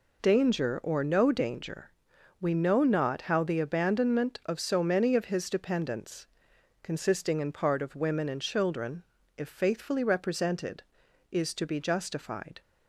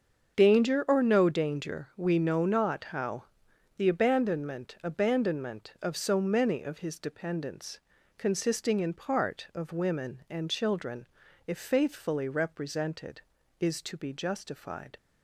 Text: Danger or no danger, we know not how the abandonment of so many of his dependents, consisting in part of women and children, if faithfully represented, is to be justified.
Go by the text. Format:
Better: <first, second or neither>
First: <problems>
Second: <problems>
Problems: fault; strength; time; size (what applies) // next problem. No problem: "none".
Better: first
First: none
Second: starts louder than the rest; until 1.4 s; 7 dB // pauses between "how" and "the"; noticeable; at 3.2 s; 0.52 s long // says "abandonment" twice; at 4.8 s